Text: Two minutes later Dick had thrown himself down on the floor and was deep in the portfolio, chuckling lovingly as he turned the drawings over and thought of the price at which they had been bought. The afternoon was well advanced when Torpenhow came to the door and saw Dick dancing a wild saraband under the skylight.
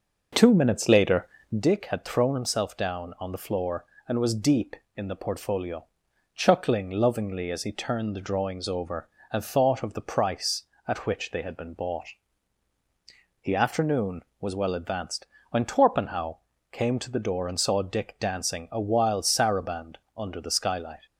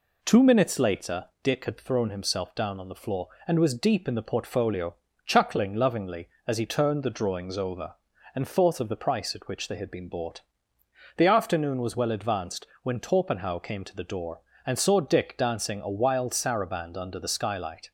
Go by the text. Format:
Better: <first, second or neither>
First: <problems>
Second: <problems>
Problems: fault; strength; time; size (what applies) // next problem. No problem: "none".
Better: second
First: starts louder than the rest; noticeable; until 1.6 s; 5.5 dB // pauses between "later" and "Dick"; slight; at 1.2 s; 0.32 s long // pauses between "advanced" and "when"; slight; at 15.2 s; 0.24 s long // pauses between "Torpenhow" and "came"; slight; at 16.3 s; 0.34 s long // pauses between "saraband" and "under"; slight; at 19.9 s; 0.20 s long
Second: pauses between "later" and "Dick"; slight; at 1.2 s; 0.16 s long // pauses between "advanced" and "when"; slight; at 12.6 s; 0.18 s long